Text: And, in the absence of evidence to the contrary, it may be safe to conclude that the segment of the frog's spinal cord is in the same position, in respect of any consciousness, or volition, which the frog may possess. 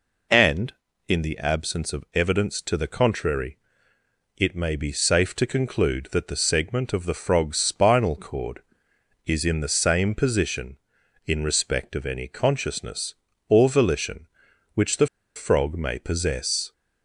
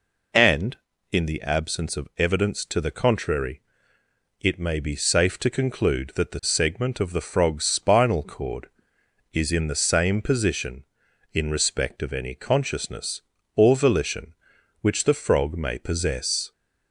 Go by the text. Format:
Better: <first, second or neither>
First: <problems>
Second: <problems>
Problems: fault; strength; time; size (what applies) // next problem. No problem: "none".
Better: second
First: pauses between "the" and "frog"; slight; at 15.0 s; 0.29 s long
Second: none